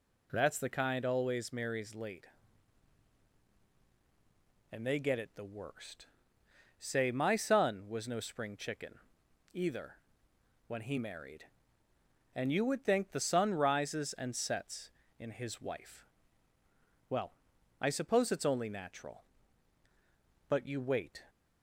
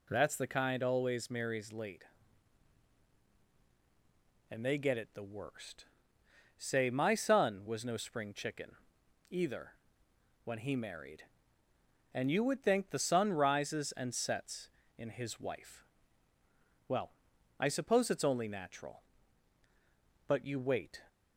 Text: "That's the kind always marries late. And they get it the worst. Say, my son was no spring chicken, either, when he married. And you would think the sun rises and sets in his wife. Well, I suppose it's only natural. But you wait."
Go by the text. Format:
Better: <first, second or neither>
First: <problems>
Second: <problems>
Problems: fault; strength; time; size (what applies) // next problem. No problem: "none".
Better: neither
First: none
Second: none